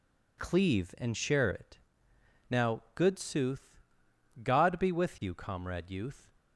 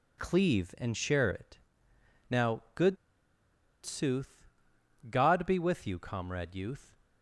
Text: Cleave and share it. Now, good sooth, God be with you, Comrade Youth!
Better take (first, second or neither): first